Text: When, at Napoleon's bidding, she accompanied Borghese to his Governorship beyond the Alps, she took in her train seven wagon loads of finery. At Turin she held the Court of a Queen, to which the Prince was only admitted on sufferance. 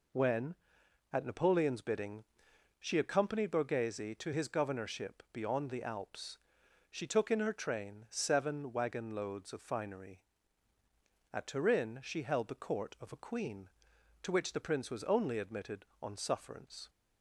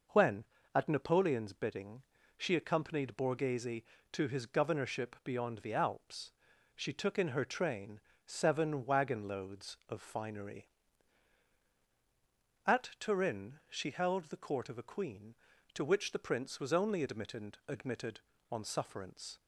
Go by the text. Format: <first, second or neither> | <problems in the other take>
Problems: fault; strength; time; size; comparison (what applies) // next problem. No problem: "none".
first | pauses between "train" and "seven"; slight; at 7.9 s; 0.26 s long // says "admitted" twice; at 17.6 s